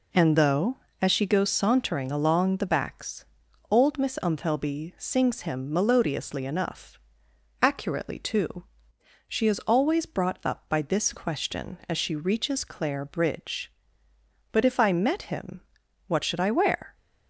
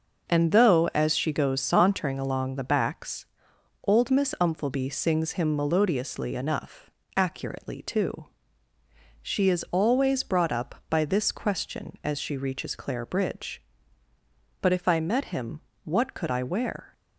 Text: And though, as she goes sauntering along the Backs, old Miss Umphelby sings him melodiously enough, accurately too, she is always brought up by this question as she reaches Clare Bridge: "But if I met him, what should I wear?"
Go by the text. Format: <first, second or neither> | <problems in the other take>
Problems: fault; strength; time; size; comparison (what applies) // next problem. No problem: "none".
first | says "could" for "should"; at 16.1 s